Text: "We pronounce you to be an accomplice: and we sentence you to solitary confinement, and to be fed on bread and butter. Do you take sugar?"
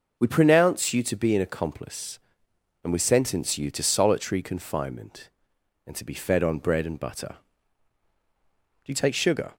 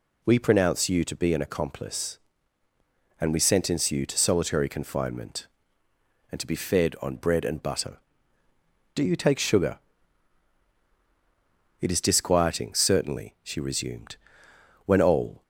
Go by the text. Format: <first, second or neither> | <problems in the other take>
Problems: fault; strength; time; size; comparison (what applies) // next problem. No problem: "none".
first | goes on to say "It is disquieting certainly she resumed when all"; strong; from 11.8 s on; 3.6 s long